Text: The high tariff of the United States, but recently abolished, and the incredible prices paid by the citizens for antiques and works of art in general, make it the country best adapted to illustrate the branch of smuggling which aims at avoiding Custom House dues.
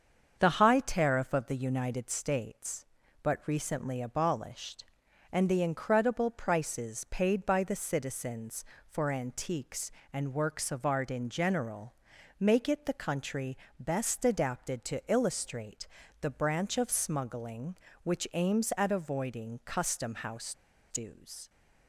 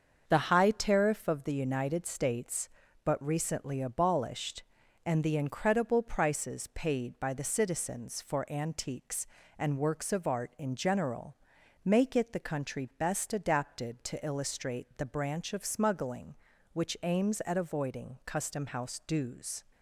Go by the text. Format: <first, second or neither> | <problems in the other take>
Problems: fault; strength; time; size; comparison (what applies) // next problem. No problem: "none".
second | starts louder than the rest; until 1.4 s; 7 dB; also in the second // pauses between "country" and "best"; slight; at 13.5 s; 0.22 s long // pauses between "illustrate" and "the"; slight; at 15.8 s; 0.32 s long // pauses between "House" and "dues"; at 20.5 s; 0.37 s long